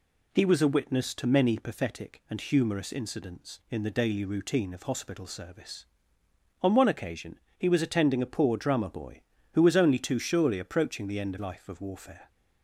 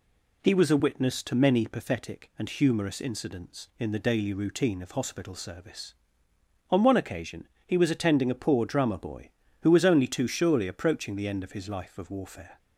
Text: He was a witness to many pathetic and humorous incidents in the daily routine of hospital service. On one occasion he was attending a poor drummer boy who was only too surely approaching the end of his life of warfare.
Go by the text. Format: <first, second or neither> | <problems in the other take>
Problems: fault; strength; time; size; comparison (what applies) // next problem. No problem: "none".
second | pauses between "occasion" and "he"; slight; at 7.4 s; 0.18 s long; slight in the second // skips "his"; at 11.3 s